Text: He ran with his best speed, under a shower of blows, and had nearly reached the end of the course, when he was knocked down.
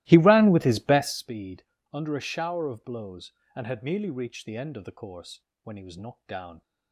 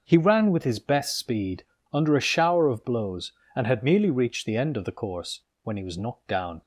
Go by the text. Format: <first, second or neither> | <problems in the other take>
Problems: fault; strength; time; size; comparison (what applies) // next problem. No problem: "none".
second | starts louder than the rest; strong; until 1.3 s; 17.5 dB